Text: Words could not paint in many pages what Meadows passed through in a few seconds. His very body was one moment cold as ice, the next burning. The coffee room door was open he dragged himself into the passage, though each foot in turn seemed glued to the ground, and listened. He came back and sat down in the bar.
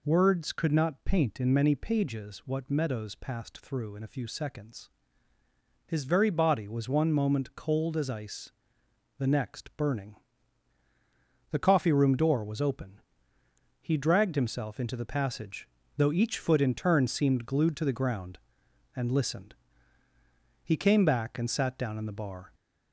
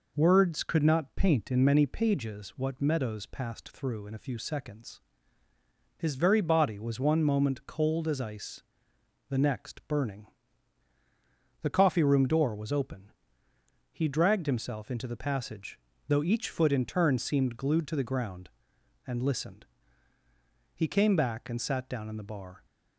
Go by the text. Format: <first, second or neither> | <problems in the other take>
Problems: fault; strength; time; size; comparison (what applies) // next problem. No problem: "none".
second | gets louder; slight; throughout; 3 dB // pauses between "open" and "he"; noticeable; at 12.9 s; 0.80 s long; noticeable in the second